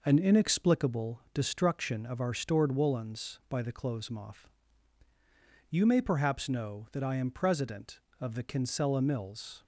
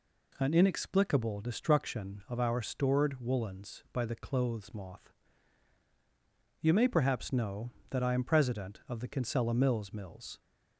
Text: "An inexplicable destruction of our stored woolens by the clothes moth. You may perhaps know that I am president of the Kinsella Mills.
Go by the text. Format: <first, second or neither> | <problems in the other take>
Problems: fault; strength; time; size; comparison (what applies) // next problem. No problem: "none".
first | says "Mills" twice; at 9.9 s